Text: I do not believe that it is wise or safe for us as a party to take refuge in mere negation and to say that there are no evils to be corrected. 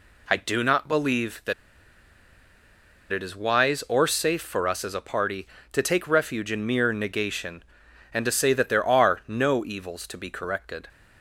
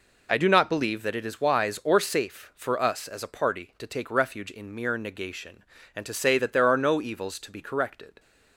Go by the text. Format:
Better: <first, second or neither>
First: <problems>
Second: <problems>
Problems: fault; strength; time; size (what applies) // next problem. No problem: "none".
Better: second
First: pauses between "that" and "it"; strong; at 1.5 s; 1.5 s long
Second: none